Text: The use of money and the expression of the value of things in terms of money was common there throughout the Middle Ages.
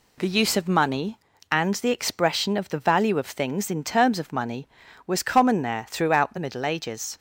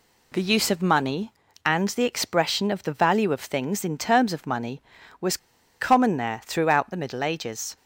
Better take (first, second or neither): first